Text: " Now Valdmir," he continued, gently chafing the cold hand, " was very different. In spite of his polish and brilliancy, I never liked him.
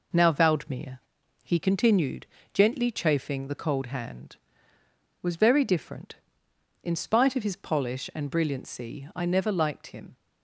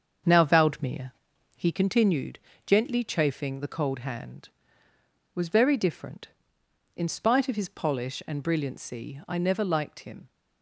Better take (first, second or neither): first